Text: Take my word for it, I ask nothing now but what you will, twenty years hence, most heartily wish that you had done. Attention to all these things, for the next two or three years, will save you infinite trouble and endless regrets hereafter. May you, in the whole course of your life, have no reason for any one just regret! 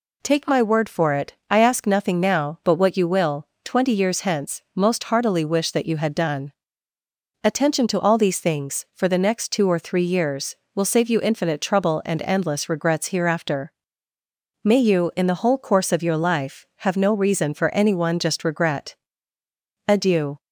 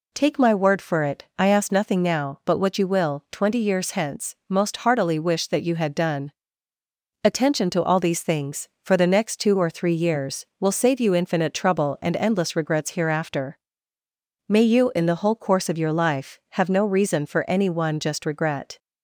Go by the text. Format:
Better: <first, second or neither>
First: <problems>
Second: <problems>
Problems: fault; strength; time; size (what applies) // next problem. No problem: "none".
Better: second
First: goes on to say "Adieu"; from 19.8 s on; 0.52 s long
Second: none